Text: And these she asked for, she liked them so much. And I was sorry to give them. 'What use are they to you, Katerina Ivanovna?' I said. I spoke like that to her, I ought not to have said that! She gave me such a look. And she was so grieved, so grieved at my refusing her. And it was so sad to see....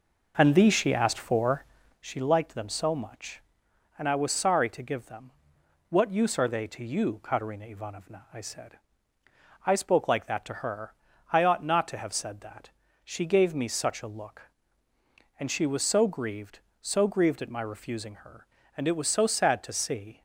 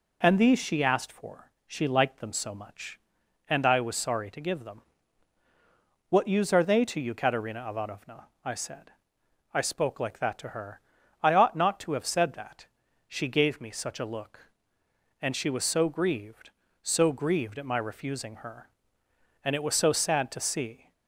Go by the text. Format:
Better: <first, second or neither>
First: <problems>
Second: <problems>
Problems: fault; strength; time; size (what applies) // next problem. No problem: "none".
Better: second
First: starts louder than the rest; noticeable; until 2.1 s; 5 dB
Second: none